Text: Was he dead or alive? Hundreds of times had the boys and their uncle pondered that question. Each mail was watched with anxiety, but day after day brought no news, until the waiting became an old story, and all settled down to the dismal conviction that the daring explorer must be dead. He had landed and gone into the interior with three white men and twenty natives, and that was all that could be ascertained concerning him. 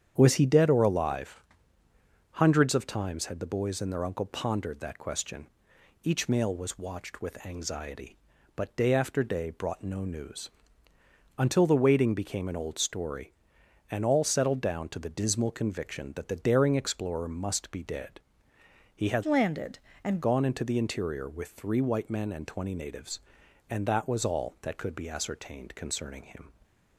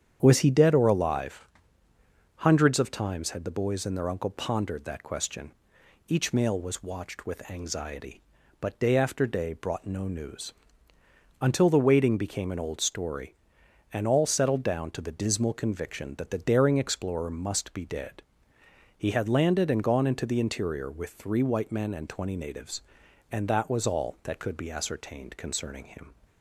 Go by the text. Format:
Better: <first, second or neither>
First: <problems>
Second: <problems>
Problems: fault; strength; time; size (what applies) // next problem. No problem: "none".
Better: second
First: starts louder than the rest; strong; until 1.1 s; 8.5 dB // changes voice from "landed" to "and"; from 19.2 to 20.2 s; 1.0 s long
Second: starts louder than the rest; strong; until 1.2 s; 8.5 dB